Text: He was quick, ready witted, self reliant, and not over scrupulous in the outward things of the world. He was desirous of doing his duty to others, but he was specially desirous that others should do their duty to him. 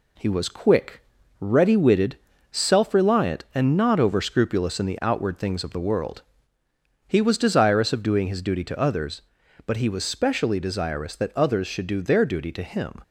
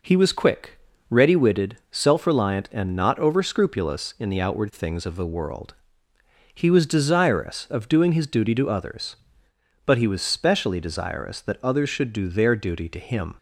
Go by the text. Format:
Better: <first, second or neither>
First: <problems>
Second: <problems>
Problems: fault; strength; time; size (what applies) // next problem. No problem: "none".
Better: neither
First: none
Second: none